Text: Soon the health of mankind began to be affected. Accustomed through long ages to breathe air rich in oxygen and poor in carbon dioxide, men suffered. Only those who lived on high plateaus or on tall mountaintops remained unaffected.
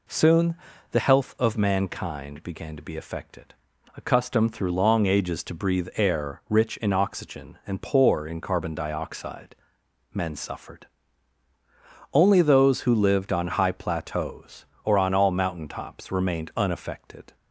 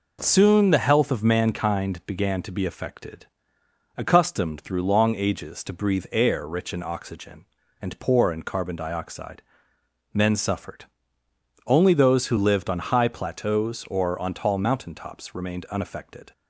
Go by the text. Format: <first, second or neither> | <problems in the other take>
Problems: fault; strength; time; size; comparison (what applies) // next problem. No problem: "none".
second | pauses between "Soon" and "the"; slight; at 0.5 s; 0.36 s long // says "all" for "tall"; at 15.1 s